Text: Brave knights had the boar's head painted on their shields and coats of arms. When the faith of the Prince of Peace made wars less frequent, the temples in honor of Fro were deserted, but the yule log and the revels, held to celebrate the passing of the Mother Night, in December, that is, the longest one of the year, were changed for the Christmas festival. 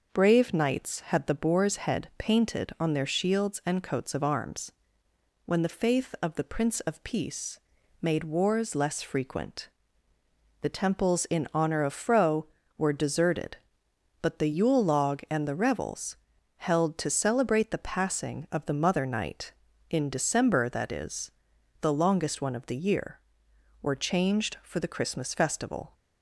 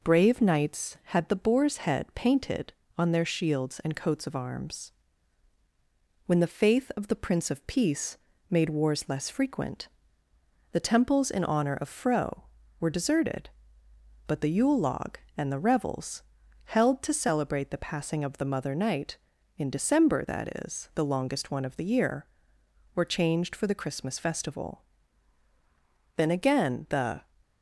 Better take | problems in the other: first | pauses between "Peace" and "made"; slight; at 8.1 s; 0.34 s long; also in the first // goes on to say "Then again the"; noticeable; from 26.1 s on; 1.0 s long

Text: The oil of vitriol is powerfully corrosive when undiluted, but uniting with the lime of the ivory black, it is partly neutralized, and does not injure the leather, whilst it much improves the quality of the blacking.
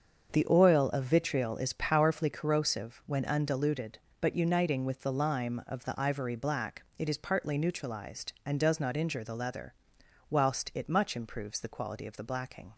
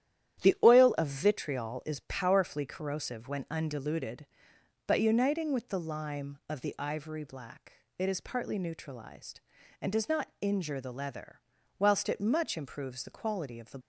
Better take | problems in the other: first | starts louder than the rest; strong; until 1.5 s; 11 dB; also in the first // stops before "blacking"; at 13.8 s

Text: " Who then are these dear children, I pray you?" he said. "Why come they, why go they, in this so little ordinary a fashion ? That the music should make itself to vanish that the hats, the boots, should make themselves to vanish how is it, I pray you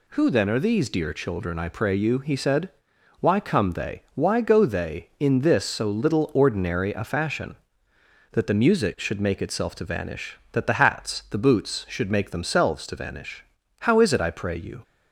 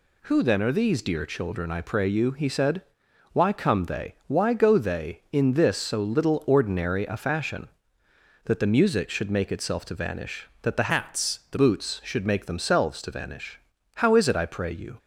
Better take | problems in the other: first | changes voice from "hats" to "the"; from 10.8 to 11.5 s; 0.7 s long // pauses between "vanish" and "how"; at 13.5 s; 0.40 s long; also in the first

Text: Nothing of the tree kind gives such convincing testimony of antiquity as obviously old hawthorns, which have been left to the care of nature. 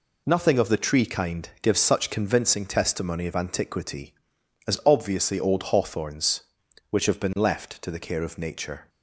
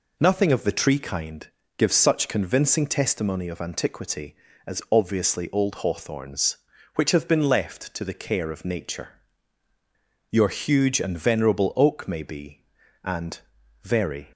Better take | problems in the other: first | pauses between "kind" and "gives"; slight; at 1.4 s; 0.30 s long // goes on to say "Your huge and venerable oak may be and very"; strong; from 10.3 s on; 3.9 s long

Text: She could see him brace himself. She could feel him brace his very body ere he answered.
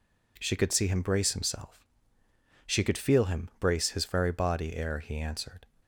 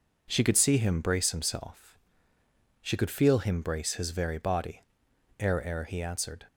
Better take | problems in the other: first | pauses between "body" and "ere"; noticeable; at 4.8 s; 0.56 s long // says "ere" twice; at 5.6 s

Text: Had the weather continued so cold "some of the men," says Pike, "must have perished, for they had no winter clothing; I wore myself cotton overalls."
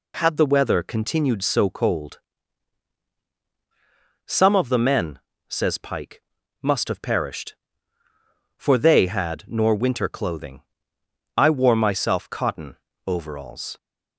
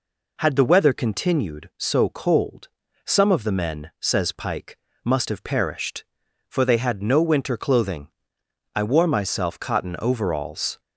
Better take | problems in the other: second | pauses between "cold" and "some"; strong; at 2.1 s; 2.0 s long; also in the second // says "nor" for "no"; at 9.4 s // pauses between "cotton" and "overalls"; slight; at 12.7 s; 0.28 s long

